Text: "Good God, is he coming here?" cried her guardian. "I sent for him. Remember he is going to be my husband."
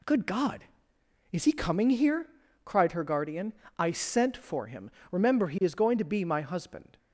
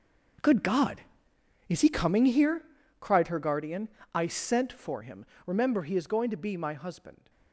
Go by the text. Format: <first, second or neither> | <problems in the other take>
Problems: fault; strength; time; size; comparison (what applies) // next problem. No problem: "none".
first | gets quieter; strong; throughout; 16 dB